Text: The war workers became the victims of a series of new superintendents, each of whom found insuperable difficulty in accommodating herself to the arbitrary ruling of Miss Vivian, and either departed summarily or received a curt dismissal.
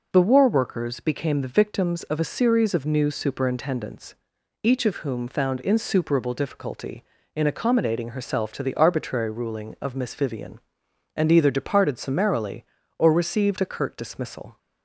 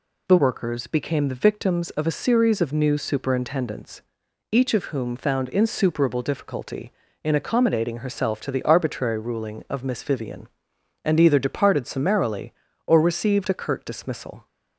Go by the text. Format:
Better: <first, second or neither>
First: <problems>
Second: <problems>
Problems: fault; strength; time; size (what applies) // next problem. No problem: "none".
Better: first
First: none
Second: skips "war"; at 0.3 s